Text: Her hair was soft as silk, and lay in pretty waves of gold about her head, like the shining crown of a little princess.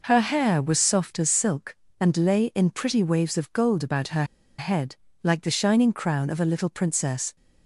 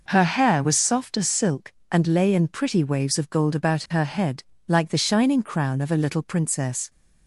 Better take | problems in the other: second | pauses between "her" and "head"; slight; at 4.2 s; 0.34 s long

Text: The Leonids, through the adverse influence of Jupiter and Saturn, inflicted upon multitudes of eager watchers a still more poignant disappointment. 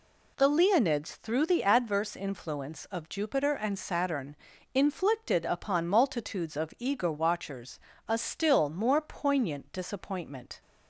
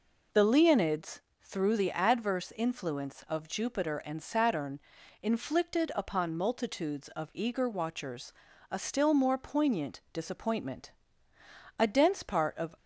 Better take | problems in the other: first | pauses between "watchers" and "a"; at 8.3 s; 0.38 s long; slight in the first // goes on to say "A dense part of"; noticeable; from 11.7 s on; 0.98 s long

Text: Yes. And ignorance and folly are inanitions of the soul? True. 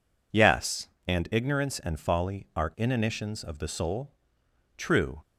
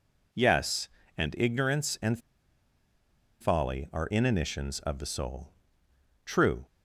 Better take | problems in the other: first | pauses between "and" and "folly"; at 2.1 s; 1.2 s long

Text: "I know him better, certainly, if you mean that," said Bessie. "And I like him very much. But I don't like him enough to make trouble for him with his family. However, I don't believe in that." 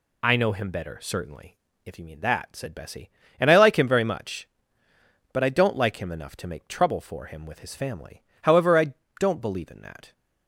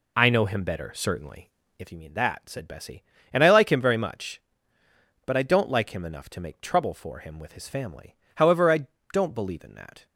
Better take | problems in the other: first | starts louder than the rest; slight; until 2.0 s; 3 dB // pauses between "I" and "don't"; slight; at 8.8 s; 0.28 s long; slight in the first

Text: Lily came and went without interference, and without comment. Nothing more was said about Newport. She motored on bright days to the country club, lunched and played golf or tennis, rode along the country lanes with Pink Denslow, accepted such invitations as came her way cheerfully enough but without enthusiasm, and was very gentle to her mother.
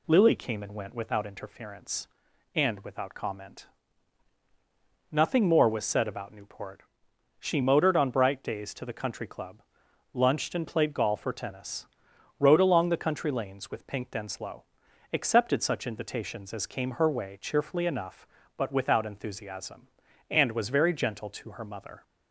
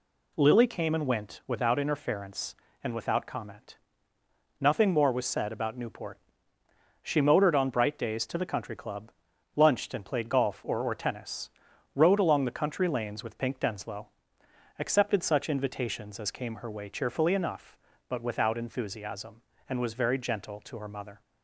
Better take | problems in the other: first | says "or" twice; at 10.8 s

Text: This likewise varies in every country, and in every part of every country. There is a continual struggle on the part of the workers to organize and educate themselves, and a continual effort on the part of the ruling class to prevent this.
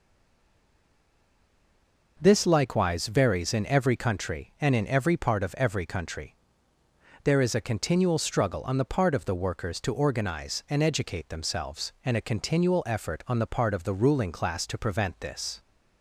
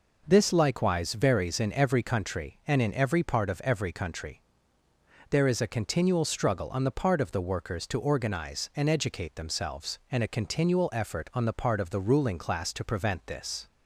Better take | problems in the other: second | stays silent before the first word; until 2.1 s; 2.1 s long

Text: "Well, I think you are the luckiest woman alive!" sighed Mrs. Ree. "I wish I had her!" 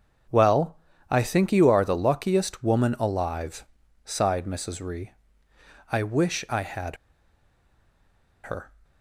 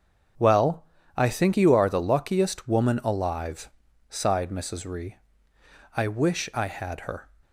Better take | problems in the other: second | starts louder than the rest; until 1.6 s; 7 dB; also in the second // pauses between "had" and "her"; strong; at 6.9 s; 1.4 s long

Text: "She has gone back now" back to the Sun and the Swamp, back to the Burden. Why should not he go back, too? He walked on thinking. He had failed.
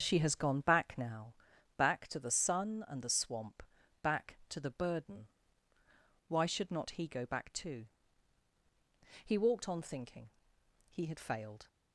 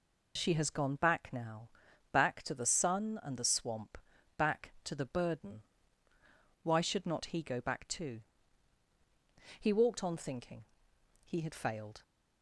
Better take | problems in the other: second | starts louder than the rest; until 1.4 s; 7 dB // pauses between "now" and "back"; at 1.3 s; 0.42 s long; also in the second

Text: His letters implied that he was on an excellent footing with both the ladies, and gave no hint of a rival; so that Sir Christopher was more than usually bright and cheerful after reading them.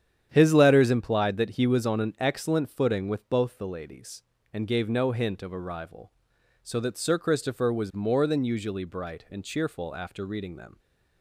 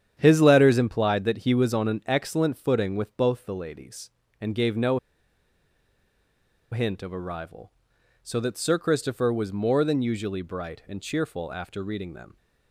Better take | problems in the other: first | starts louder than the rest; strong; until 1.1 s; 9 dB; strong in the first // pauses between "no" and "hint"; strong; at 4.9 s; 1.7 s long

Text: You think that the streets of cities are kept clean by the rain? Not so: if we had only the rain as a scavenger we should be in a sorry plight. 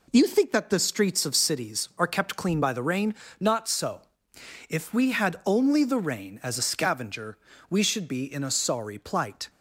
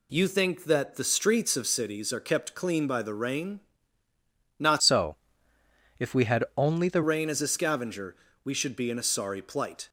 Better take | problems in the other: first | changes voice from "so" to "the"; from 4.8 to 7.0 s; 2.2 s long // pauses between "scavenger" and "we"; slight; at 8.1 s; 0.30 s long; slight in the first

